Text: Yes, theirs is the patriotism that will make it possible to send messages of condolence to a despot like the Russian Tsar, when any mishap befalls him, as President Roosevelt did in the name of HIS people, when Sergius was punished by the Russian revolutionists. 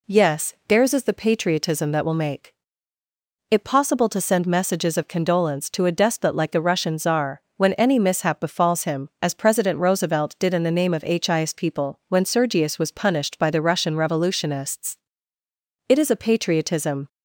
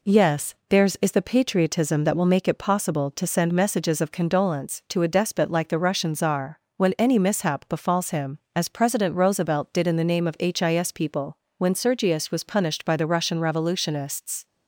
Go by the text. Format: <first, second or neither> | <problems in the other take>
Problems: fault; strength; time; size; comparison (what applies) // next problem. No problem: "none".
second | pauses between "make" and "it"; noticeable; at 2.5 s; 0.98 s long // goes on to say "It is a patriotism"; noticeable; from 15.8 s on; 1.2 s long